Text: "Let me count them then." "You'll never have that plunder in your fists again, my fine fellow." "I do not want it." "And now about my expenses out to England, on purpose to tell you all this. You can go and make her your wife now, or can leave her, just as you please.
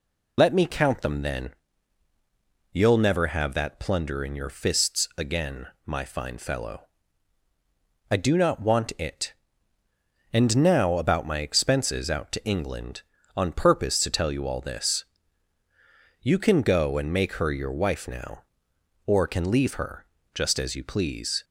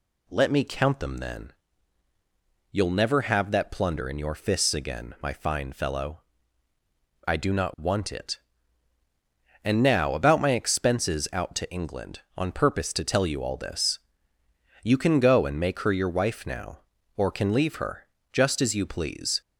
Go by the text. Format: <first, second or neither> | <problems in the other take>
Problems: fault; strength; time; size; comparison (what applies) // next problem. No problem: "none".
second | loses the start of "Let"; at 0.3 s; 50 ms